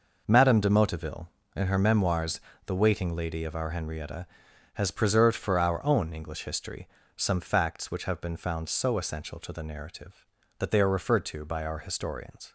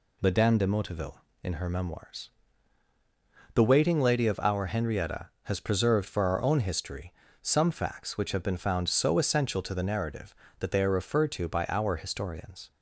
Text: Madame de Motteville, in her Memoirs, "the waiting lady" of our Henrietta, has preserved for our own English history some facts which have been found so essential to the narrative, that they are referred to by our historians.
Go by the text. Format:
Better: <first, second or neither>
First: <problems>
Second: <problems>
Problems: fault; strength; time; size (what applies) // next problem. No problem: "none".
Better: first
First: pauses between "history" and "some"; slight; at 6.8 s; 0.30 s long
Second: skips "English"; at 6.6 s // pauses between "history" and "some"; slight; at 7.1 s; 0.30 s long